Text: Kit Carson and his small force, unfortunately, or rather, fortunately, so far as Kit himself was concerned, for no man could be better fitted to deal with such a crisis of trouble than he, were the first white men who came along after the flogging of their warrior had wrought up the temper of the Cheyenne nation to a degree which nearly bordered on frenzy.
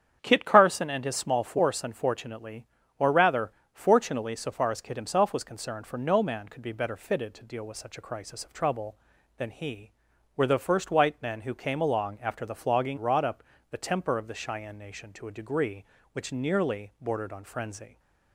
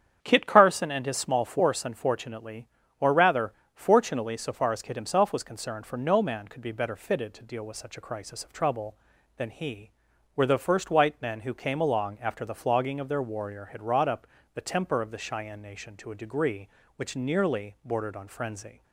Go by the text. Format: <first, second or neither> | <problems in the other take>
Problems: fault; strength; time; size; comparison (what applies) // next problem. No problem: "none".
second | starts louder than the rest; strong; until 1.2 s; 8.5 dB; strong in the second // skips "of their warrior had"; at 12.9 s // pauses between "up" and "the"; slight; at 13.4 s; 0.28 s long; slight in the second